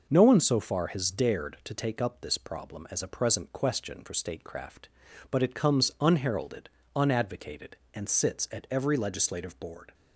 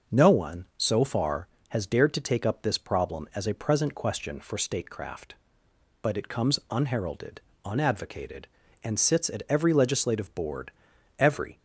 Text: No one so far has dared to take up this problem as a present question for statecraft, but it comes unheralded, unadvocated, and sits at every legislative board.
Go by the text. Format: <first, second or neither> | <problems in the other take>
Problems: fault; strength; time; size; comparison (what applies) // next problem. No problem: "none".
first | goes on to say "Every"; slight; from 11.1 s on; 0.38 s long